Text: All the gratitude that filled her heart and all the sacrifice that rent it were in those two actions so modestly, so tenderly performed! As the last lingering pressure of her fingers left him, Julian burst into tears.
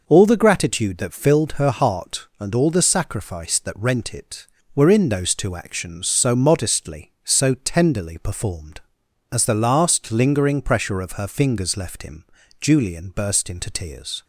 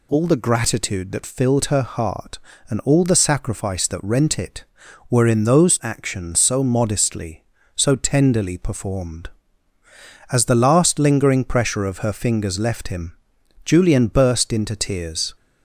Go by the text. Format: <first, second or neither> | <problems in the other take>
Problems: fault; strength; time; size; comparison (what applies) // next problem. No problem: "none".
first | skips "two"; at 5.8 s